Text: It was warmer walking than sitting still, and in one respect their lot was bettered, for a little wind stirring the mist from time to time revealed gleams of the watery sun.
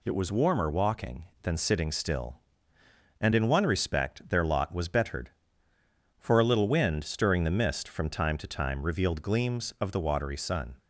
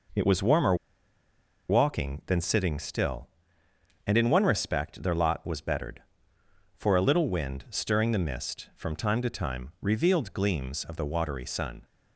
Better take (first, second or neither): first